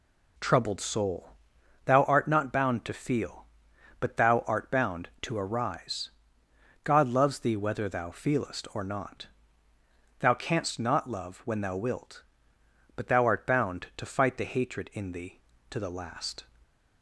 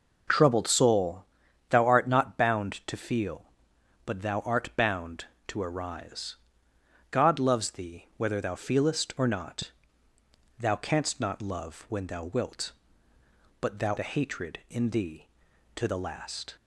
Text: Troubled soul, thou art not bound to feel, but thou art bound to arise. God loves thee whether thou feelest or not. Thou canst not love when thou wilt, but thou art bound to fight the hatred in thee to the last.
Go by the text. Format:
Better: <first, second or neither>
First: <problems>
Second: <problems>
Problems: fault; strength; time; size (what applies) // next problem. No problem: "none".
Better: first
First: none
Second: skips "art bound to fight"; at 13.9 s